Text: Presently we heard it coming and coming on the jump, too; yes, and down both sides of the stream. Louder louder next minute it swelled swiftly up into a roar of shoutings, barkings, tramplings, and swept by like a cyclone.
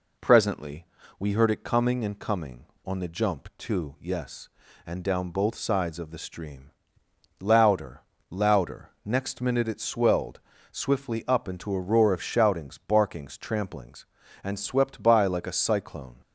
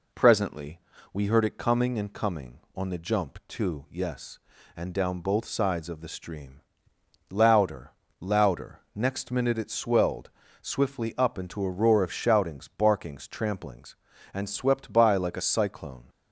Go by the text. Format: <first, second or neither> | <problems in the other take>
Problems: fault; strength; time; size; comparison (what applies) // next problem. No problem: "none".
neither | pauses between "Presently" and "we"; slight; the same in both // pauses between "Louder" and "louder"; slight; the same in both // pauses between "louder" and "next"; slight; the same in both // pauses between "swelled" and "swiftly"; slight; the same in both